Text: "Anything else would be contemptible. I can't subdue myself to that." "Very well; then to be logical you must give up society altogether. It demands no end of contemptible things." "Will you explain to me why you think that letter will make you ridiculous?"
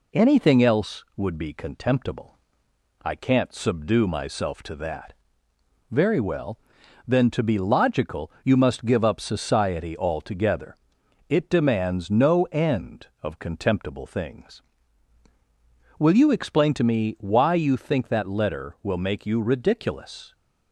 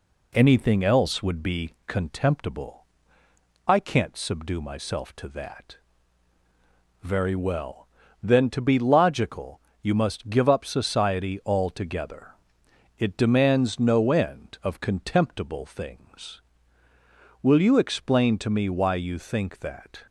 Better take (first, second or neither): first